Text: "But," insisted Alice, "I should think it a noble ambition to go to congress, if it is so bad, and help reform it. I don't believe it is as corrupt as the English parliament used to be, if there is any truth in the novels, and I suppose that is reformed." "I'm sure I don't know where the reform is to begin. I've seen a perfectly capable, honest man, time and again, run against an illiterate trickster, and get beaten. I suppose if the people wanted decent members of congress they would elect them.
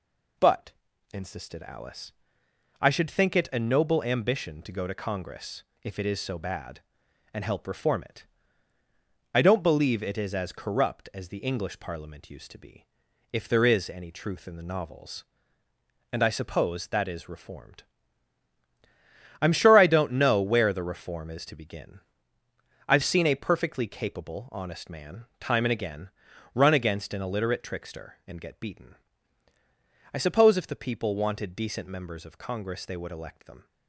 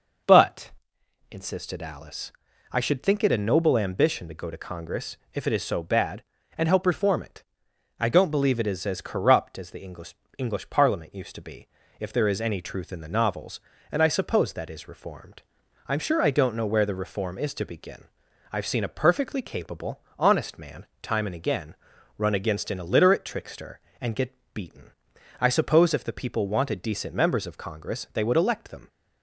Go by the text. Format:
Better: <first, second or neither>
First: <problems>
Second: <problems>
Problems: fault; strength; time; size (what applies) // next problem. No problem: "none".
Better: first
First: none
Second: says "English" twice; at 10.3 s // pauses between "get" and "beaten"; slight; at 24.3 s; 0.20 s long